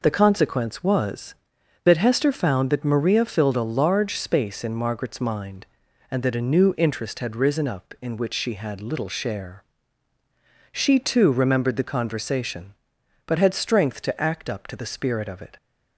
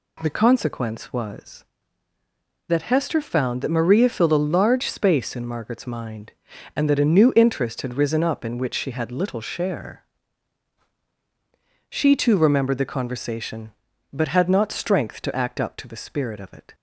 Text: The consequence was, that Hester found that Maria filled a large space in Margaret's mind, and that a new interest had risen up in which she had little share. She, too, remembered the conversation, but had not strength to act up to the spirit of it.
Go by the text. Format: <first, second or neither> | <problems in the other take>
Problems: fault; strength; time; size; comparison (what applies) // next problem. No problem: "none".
second | skips "not"; at 13.5 s